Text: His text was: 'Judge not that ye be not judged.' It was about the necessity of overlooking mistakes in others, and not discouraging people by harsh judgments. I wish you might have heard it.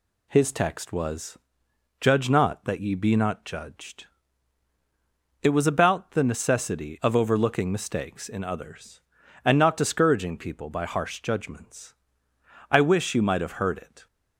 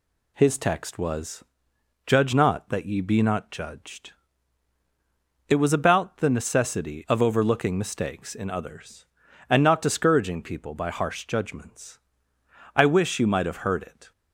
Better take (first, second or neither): neither